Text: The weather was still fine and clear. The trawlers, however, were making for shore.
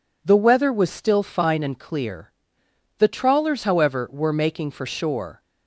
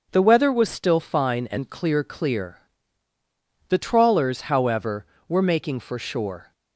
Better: first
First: none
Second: says "clear" twice; at 2.0 s

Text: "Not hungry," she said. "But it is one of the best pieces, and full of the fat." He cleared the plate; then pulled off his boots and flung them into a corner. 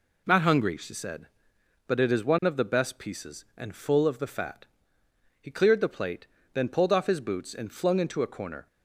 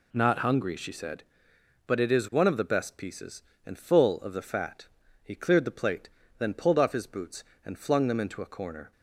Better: second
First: skips "them"; at 8.0 s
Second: none

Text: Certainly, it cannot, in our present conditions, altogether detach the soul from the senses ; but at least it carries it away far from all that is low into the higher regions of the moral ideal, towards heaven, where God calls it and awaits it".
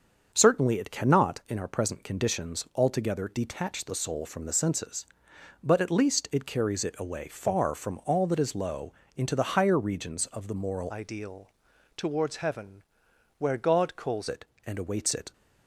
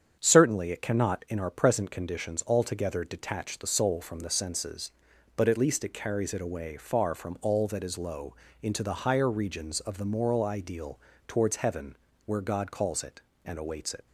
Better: second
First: starts louder than the rest; until 1.3 s; 6.5 dB // pauses between "low" and "into"; slight; at 8.9 s; 0.20 s long // changes voice from "ideal" to "calls"; from 10.8 to 14.2 s; 3.4 s long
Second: starts louder than the rest; strong; until 1.2 s; 7.5 dB // pauses between "low" and "into"; slight; at 8.3 s; 0.28 s long

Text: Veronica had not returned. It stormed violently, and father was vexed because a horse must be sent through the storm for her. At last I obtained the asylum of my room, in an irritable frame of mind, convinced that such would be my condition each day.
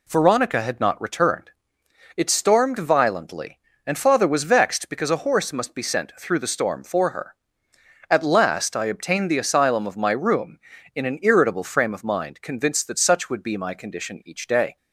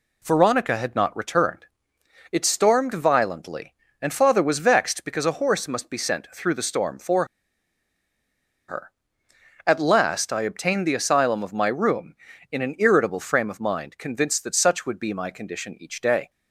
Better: first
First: none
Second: pauses between "for" and "her"; strong; at 7.2 s; 1.4 s long

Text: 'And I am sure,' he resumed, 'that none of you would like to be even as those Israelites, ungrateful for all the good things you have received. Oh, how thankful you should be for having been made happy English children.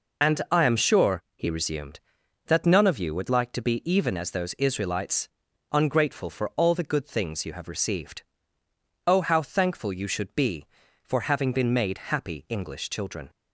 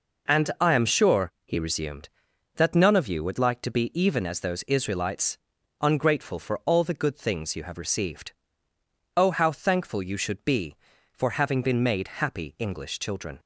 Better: second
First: loses the start of "And"; at 0.2 s; 35 ms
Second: none

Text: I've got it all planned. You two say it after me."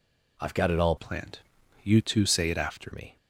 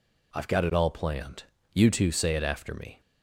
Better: second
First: changes voice from "planned" to "after"; from 0.9 to 2.9 s; 2.0 s long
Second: none

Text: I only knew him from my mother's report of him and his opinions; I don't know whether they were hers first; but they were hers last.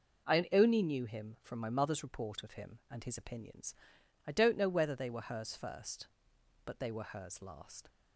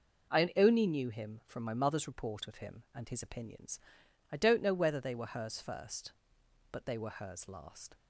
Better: neither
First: none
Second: none

